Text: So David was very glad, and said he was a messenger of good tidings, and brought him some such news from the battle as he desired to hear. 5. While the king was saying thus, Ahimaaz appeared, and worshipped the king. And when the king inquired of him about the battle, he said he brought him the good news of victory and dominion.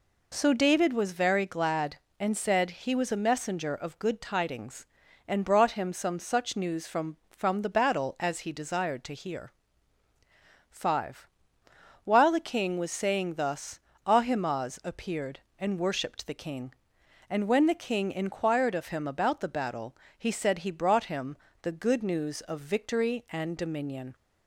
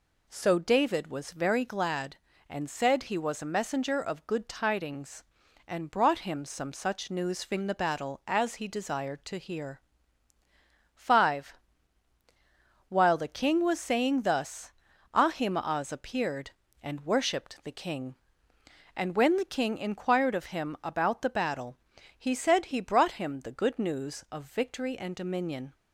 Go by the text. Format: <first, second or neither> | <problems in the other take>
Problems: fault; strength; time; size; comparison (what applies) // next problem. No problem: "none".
second | says "from" twice; at 7.2 s // pauses between "him" and "the"; slight; at 21.3 s; 0.24 s long